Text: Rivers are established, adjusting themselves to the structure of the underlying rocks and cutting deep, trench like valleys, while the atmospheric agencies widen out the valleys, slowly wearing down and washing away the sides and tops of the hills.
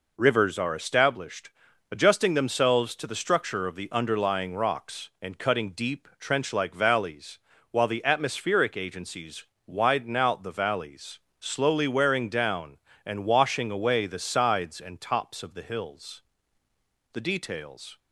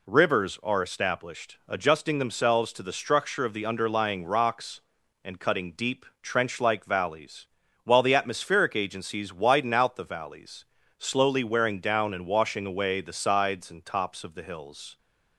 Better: second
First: pauses between "agencies" and "widen"; slight; at 9.4 s; 0.22 s long // goes on to say "The details"; noticeable; from 17.1 s on; 0.86 s long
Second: none

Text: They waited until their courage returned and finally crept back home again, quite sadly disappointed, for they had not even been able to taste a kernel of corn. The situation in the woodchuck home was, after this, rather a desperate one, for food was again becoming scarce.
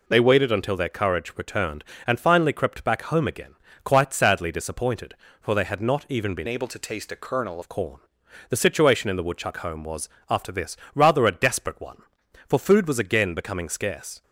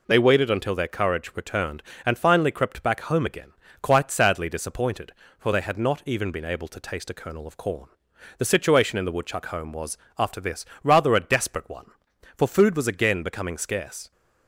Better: second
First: changes voice from "able" to "kernel"; from 6.4 to 7.5 s; 1.1 s long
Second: none

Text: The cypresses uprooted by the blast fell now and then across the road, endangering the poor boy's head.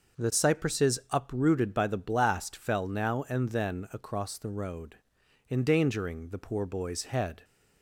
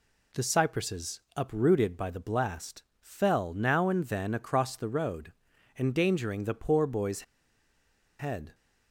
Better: first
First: none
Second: pauses between "cypresses" and "uprooted"; slight; at 1.2 s; 0.16 s long // pauses between "blast" and "fell"; slight; at 2.8 s; 0.16 s long // pauses between "boy's" and "head"; noticeable; at 7.2 s; 0.97 s long

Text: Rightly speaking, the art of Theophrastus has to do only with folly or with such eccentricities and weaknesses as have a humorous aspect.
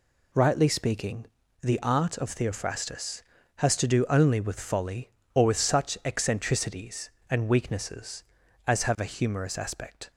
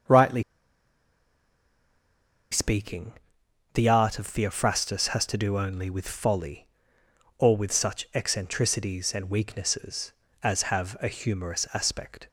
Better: first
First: none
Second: starts louder than the rest; noticeable; until 3.7 s; 6 dB // pauses between "Rightly" and "speaking"; strong; at 0.4 s; 2.0 s long

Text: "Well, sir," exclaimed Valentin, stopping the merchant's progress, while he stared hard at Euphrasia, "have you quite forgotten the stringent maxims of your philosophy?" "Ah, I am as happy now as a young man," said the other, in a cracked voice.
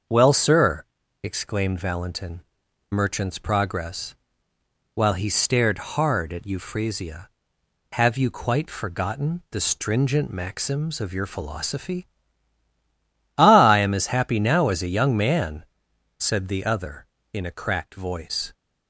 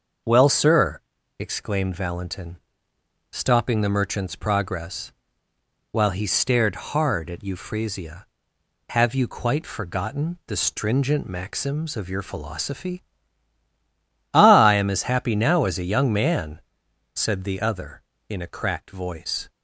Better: second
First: starts louder than the rest; until 1.4 s; 6.5 dB // skips "stopping the"; at 2.6 s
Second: starts louder than the rest; noticeable; until 1.6 s; 6 dB

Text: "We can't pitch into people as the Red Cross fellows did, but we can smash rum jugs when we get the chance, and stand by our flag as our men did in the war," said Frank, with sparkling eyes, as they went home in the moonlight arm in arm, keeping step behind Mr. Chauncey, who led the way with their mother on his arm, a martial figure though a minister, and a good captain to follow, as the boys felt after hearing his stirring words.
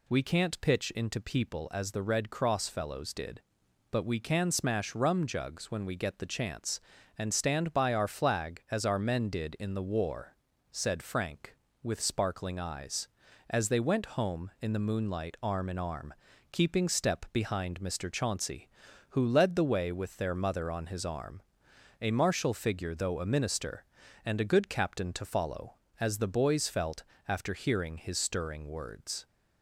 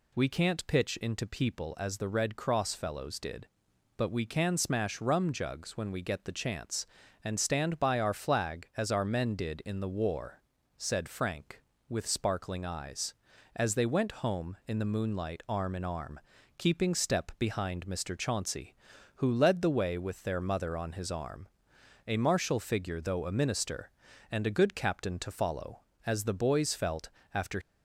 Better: first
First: pauses between "felt" and "after"; slight; at 27.0 s; 0.24 s long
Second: pauses between "felt" and "after"; slight; at 27.0 s; 0.24 s long // stops before "hearing his stirring words"; at 27.6 s

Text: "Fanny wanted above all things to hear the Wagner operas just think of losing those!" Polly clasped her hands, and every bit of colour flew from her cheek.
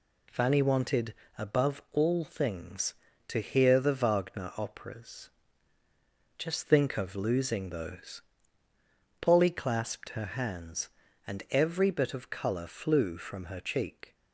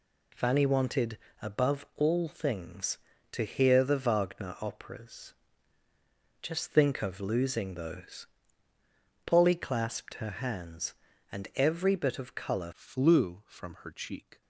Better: first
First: pauses between "wanted" and "above"; slight; at 1.1 s; 0.22 s long // pauses between "operas" and "just"; at 5.2 s; 1.0 s long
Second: pauses between "wanted" and "above"; slight; at 1.1 s; 0.22 s long // pauses between "operas" and "just"; at 5.3 s; 1.0 s long // changes voice at "flew"; from 12.7 s on; 1.7 s long

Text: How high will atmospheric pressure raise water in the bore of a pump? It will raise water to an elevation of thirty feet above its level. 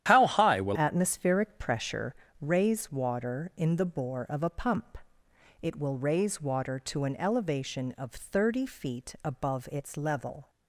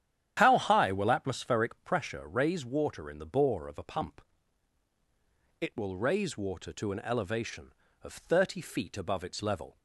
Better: second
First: starts louder than the rest; strong; until 1.0 s; 11 dB // changes voice at "atmospheric"; from 0.7 s on; 9.7 s long // pauses between "pressure" and "raise"; slight; at 2.1 s; 0.28 s long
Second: starts louder than the rest; strong; until 1.3 s; 10 dB

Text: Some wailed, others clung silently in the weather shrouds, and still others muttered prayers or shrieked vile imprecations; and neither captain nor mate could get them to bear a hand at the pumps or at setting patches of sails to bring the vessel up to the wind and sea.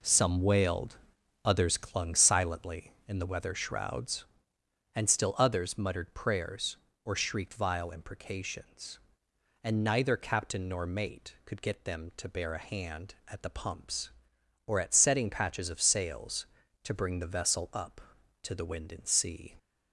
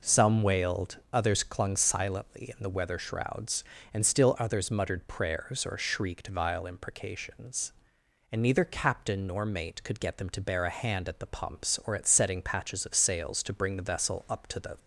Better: first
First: none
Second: stops before "wind and sea"; at 14.7 s

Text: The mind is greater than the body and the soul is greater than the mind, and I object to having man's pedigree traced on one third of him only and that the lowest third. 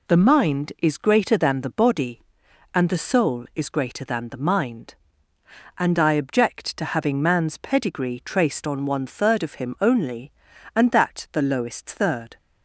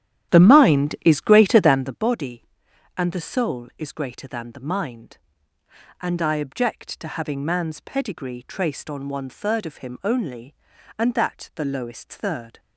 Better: first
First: none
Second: starts louder than the rest; strong; until 2.0 s; 11.5 dB

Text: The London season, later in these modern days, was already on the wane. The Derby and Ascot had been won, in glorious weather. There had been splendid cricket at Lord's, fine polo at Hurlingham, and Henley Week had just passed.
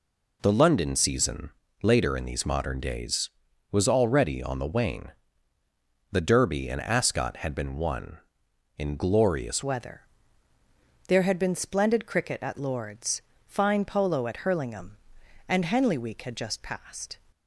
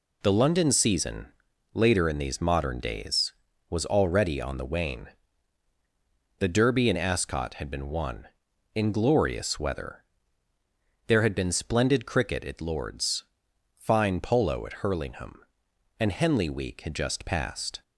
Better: second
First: changes voice at "weather"; from 9.6 s on; 7.5 s long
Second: none

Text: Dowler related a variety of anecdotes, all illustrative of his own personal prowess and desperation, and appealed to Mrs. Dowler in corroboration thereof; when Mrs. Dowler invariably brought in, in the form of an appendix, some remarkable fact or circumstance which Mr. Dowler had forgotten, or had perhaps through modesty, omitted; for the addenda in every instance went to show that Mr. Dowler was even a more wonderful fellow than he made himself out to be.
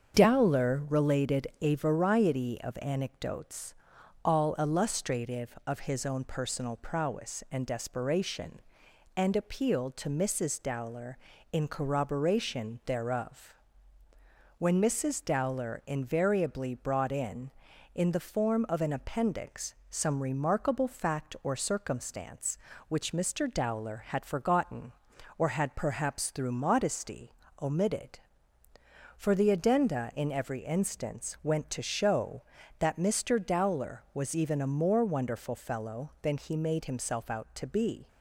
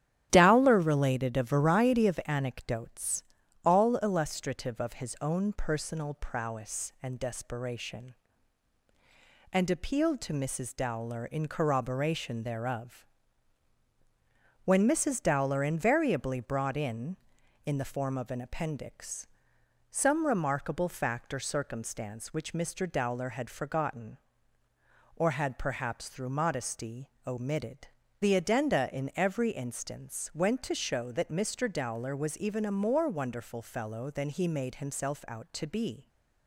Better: first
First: starts louder than the rest; strong; until 1.2 s; 7 dB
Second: starts louder than the rest; strong; until 1.3 s; 12 dB // skips "for"; at 28.0 s

